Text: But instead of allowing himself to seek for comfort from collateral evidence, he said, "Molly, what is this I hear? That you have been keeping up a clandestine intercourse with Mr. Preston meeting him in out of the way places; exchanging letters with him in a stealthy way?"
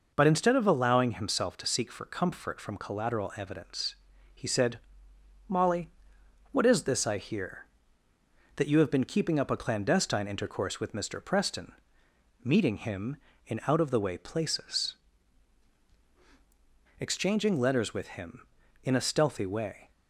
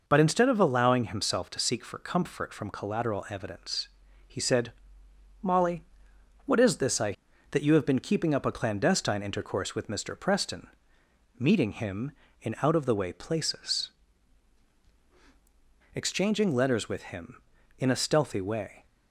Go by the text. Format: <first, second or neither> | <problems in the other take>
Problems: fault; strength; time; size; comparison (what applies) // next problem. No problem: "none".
first | skips "hear"; at 7.3 s // pauses between "Preston" and "meeting"; noticeable; at 10.6 s; 0.70 s long; noticeable in the first